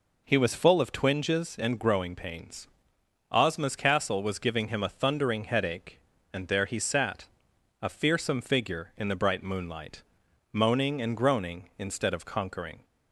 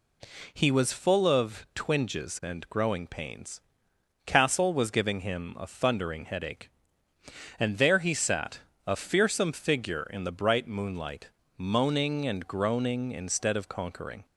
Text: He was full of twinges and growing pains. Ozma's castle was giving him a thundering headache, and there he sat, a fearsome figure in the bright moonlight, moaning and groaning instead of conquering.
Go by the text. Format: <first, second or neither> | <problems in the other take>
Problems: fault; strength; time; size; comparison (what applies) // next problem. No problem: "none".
first | skips "Ozma's"; at 3.9 s